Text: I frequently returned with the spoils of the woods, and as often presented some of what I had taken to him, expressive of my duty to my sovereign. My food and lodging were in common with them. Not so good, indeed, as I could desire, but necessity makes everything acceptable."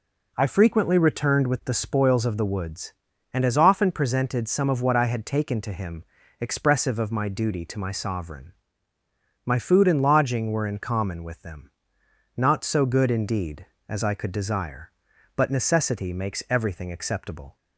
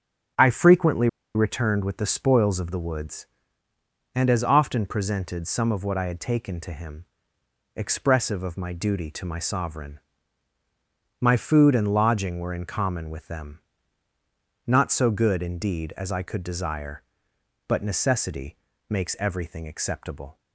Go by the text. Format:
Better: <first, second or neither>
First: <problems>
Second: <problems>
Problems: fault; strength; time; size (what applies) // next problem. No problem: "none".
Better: first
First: none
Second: starts louder than the rest; strong; until 1.6 s; 7 dB // pauses between "frequently" and "returned"; slight; at 1.0 s; 0.27 s long // pauses between "necessity" and "makes"; slight; at 18.5 s; 0.34 s long